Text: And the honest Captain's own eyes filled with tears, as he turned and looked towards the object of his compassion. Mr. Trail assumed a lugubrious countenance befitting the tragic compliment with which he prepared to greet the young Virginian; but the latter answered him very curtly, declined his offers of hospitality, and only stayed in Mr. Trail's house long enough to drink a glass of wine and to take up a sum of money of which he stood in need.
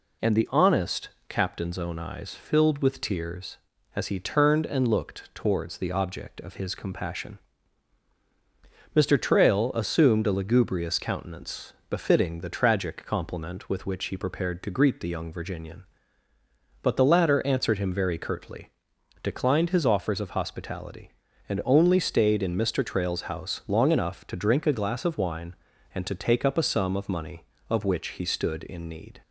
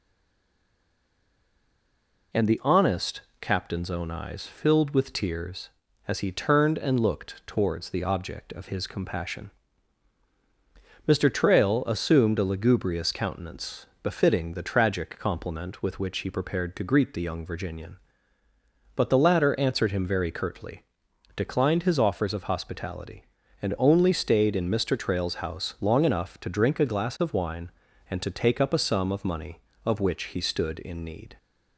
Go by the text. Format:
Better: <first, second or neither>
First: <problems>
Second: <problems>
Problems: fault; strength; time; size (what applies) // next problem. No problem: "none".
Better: first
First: pauses between "honest" and "Captain's"; slight; at 1.0 s; 0.18 s long // pauses between "countenance" and "befitting"; slight; at 11.7 s; 0.16 s long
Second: stays silent before the first word; until 2.3 s; 2.3 s long // pauses between "honest" and "Captain's"; slight; at 3.2 s; 0.18 s long // pauses between "countenance" and "befitting"; slight; at 13.8 s; 0.16 s long